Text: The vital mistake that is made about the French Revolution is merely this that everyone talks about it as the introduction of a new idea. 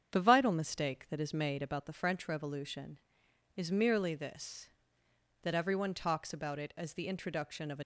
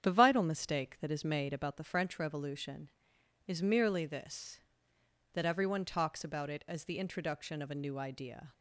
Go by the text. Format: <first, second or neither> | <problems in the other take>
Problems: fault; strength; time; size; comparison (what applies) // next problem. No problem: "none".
second | starts louder than the rest; strong; until 1.2 s; 8 dB; strong in the second // stops before "new idea"; at 7.8 s